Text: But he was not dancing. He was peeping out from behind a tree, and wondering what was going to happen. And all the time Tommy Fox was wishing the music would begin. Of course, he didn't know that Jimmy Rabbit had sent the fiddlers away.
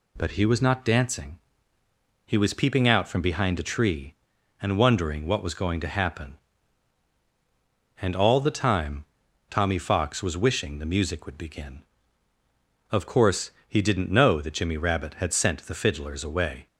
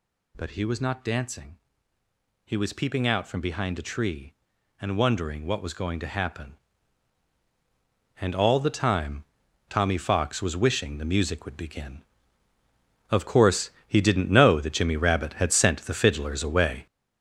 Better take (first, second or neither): first